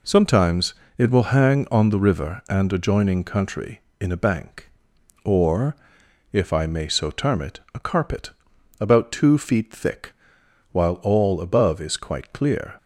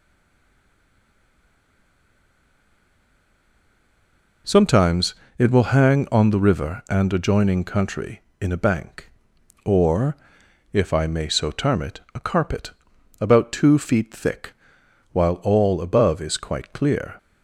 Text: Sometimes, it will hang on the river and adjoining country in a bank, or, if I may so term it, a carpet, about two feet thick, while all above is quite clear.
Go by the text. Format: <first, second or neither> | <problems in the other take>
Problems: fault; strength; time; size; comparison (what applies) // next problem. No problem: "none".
first | stays silent before the first word; strong; until 4.4 s; 4.4 s long